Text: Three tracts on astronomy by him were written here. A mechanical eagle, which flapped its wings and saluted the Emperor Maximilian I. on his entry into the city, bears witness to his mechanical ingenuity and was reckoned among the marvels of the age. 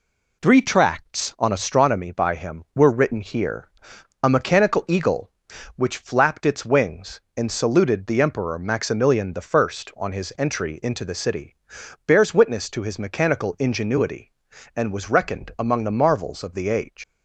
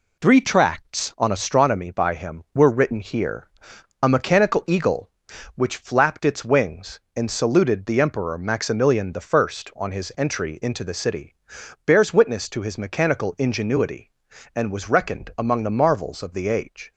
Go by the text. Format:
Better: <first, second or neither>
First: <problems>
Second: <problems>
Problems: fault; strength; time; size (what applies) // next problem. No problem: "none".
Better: second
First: leaves "age" unfinished; at 17.0 s; 90 ms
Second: none